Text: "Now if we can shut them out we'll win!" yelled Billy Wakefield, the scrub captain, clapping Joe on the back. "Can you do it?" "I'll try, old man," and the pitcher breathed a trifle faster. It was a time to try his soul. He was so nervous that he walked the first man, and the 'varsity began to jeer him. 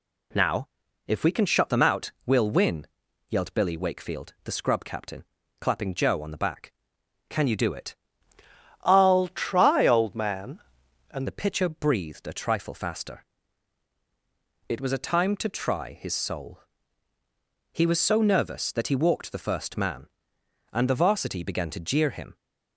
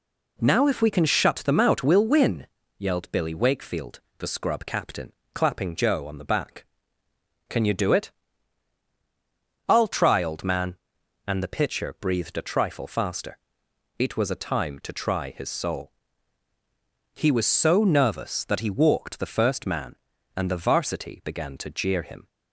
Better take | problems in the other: second | pauses between "Now" and "if"; at 0.6 s; 0.40 s long // changes voice from "I'll" to "and"; from 8.8 to 11.2 s; 2.4 s long

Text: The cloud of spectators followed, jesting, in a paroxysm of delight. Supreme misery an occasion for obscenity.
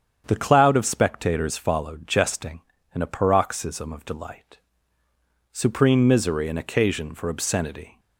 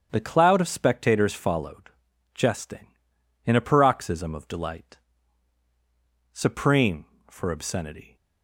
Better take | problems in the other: first | starts louder than the rest; strong; until 1.1 s; 8 dB; strong in the first // skips "misery an occasion"; at 7.1 s

